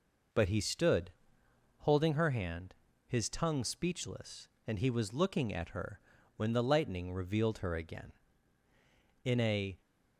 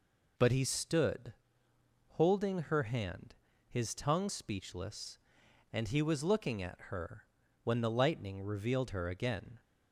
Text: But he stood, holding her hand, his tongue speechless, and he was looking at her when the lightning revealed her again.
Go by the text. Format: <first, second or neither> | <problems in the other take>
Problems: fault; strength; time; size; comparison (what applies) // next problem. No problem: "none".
second | pauses between "her" and "when"; at 5.9 s; 0.38 s long; also in the second // goes on to say "In a"; from 9.2 s on; 0.56 s long